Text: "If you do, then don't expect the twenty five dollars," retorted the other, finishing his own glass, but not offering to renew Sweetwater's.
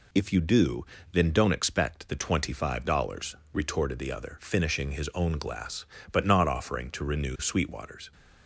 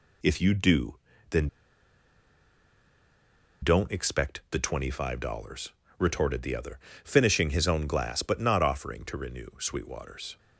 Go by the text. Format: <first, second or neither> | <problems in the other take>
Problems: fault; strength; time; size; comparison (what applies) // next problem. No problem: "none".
first | pauses between "then" and "don't"; strong; at 1.4 s; 2.1 s long